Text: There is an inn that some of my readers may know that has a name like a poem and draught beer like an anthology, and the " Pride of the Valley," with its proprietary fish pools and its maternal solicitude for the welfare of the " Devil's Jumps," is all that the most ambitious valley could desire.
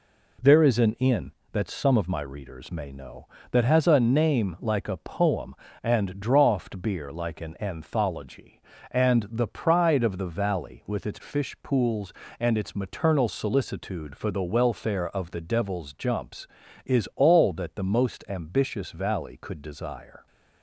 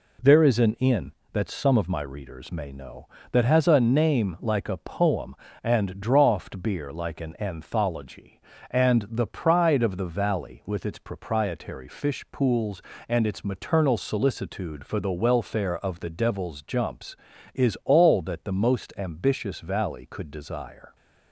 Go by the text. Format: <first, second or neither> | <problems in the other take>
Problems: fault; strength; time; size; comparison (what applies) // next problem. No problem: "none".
second | skips "proprietary"; at 11.1 s